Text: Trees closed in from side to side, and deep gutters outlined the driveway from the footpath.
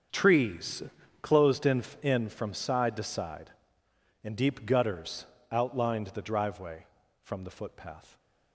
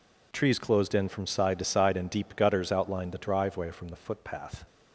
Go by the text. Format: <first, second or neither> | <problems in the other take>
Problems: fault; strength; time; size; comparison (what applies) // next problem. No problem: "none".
second | starts louder than the rest; strong; until 1.5 s; 7 dB // pauses between "Trees" and "closed"; at 0.8 s; 0.40 s long // says "in" twice; at 2.0 s // pauses between "gutters" and "outlined"; slight; at 5.2 s; 0.26 s long